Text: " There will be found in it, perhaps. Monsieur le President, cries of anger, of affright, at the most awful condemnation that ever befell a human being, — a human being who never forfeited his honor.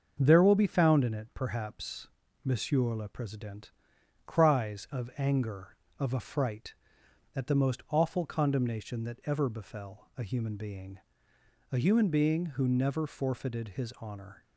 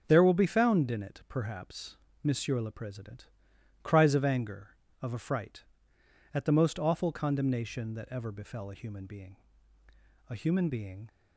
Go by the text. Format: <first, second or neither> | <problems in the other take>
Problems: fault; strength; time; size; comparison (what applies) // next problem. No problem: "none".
first | starts louder than the rest; until 1.0 s; 6 dB; also in the first // stops before "who never forfeited his honor"; at 11.0 s